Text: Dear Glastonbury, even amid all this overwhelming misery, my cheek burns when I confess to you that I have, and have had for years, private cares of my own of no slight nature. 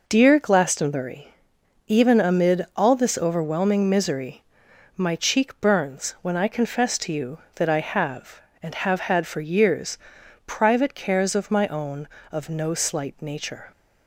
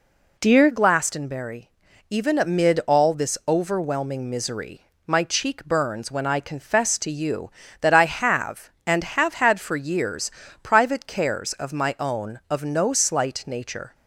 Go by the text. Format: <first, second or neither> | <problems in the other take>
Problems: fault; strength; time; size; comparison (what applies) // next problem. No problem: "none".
first | changes voice at "Glastonbury"; from 0.7 s on; 13.2 s long